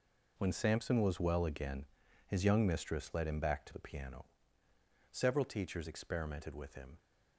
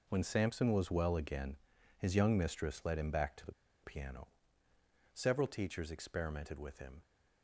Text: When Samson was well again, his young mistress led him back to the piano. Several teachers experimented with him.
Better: first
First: none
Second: pauses between "the" and "piano"; slight; at 3.5 s; 0.32 s long

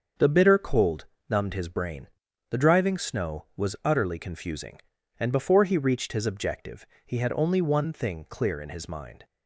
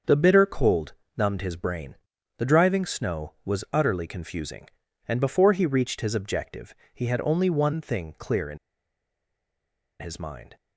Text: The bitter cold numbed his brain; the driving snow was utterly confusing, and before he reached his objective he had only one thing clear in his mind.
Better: first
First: starts louder than the rest; until 1.4 s; 6.5 dB // pauses between "cold" and "numbed"; slight; at 1.0 s; 0.24 s long // pauses between "objective" and "he"; slight; at 6.8 s; 0.20 s long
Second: starts louder than the rest; until 1.3 s; 6.5 dB // pauses between "cold" and "numbed"; slight; at 0.9 s; 0.24 s long // pauses between "objective" and "he"; slight; at 6.7 s; 0.20 s long // pauses between "in" and "his"; strong; at 8.5 s; 1.4 s long

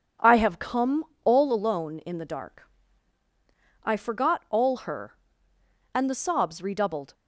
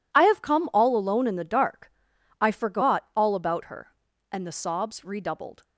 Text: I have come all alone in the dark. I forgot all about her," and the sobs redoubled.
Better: second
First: pauses between "come" and "all"; slight; at 1.0 s; 0.18 s long // skips "about"; at 4.8 s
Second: none

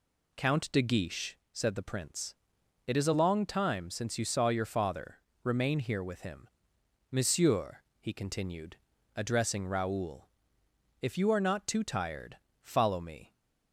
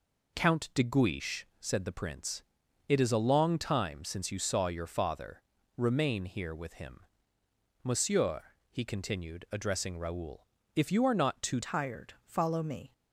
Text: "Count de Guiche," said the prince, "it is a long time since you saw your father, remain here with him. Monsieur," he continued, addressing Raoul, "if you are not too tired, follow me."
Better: first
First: none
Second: changes voice at "tired"; from 11.6 s on; 1.3 s long

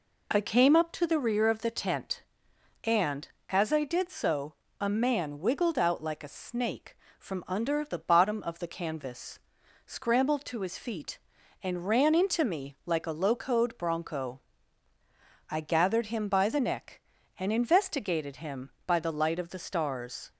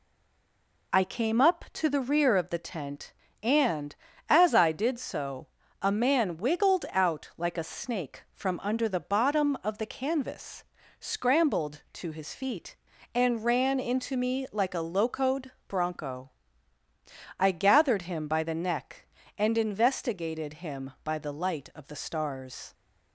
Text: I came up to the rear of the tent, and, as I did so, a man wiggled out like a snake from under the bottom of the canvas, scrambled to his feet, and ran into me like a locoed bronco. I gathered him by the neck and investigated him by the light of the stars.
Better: first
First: none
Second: stays silent before the first word; slight; until 0.9 s; 0.9 s long // pauses between "locoed" and "bronco"; slight; at 15.5 s; 0.16 s long

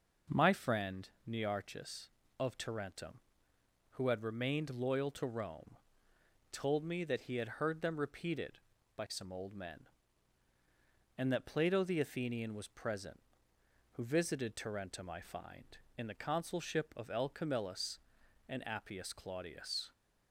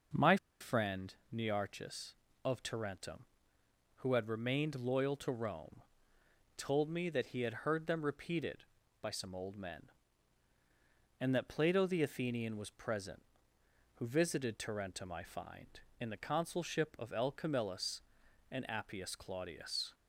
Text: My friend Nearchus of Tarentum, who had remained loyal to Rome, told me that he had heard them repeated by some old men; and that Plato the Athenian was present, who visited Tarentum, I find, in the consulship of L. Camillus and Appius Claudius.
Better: first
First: pauses between "friend" and "Nearchus"; slight; at 1.0 s; 0.18 s long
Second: pauses between "My" and "friend"; slight; at 0.3 s; 0.24 s long // pauses between "friend" and "Nearchus"; slight; at 1.1 s; 0.18 s long

